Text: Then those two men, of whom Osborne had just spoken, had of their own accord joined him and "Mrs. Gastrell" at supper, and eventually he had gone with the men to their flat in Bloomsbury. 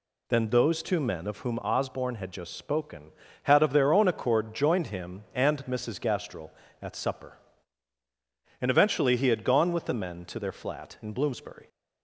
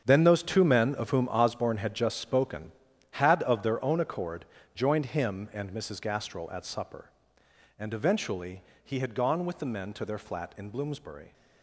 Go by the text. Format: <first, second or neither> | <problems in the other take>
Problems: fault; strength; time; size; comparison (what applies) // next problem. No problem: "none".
first | gets quieter; strong; throughout; 12.5 dB // pauses between "accord" and "joined"; slight; at 4.4 s; 0.28 s long // pauses between "eventually" and "he"; slight; at 8.6 s; 0.20 s long